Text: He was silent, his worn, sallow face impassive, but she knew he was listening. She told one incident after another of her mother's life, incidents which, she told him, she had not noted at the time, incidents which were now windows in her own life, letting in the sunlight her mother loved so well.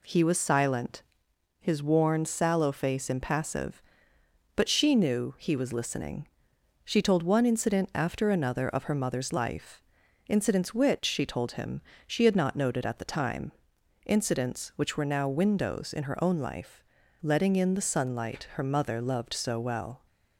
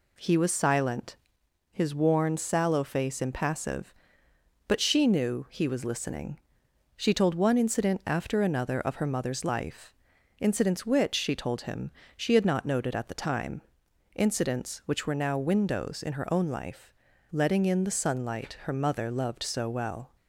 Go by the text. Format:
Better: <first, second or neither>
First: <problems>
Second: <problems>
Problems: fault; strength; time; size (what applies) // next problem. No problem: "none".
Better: neither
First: none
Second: none